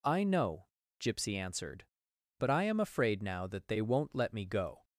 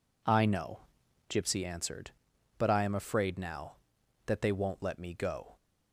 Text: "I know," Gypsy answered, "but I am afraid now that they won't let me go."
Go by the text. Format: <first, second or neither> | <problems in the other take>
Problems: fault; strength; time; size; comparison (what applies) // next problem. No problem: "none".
neither | none